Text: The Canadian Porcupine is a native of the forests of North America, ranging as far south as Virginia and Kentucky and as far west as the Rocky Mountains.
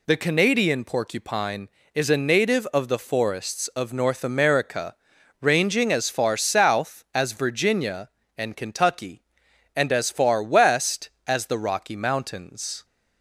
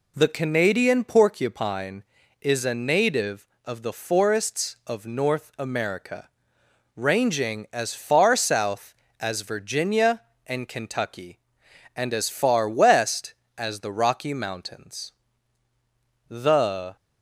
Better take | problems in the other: first | goes on to say "The"; noticeable; from 16.2 s on; 0.68 s long

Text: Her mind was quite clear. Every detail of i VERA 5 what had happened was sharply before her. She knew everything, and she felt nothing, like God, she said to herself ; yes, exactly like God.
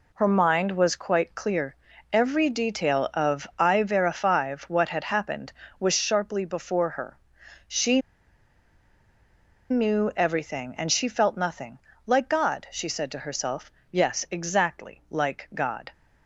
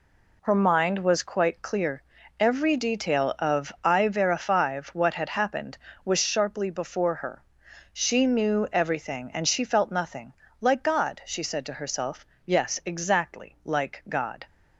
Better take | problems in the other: second | pauses between "She" and "knew"; strong; at 8.0 s; 1.7 s long

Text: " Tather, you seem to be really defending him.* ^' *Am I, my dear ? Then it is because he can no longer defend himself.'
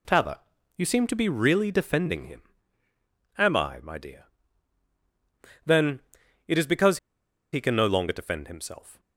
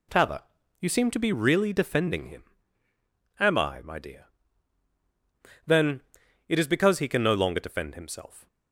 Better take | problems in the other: second | pauses between "Then" and "it"; noticeable; at 5.9 s; 0.46 s long; noticeable in the second // pauses between "because" and "he"; noticeable; at 6.9 s; 0.54 s long

